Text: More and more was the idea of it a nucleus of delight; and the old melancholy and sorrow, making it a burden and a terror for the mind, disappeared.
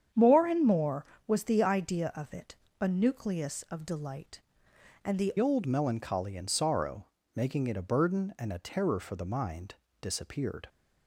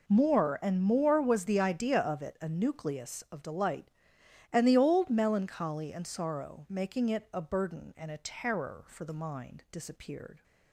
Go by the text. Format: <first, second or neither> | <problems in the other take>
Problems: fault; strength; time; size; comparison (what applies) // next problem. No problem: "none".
second | starts louder than the rest; strong; until 1.3 s; 8.5 dB // pauses between "it" and "a"; slight; at 2.5 s; 0.26 s long // changes voice at "old"; from 5.3 s on; 5.3 s long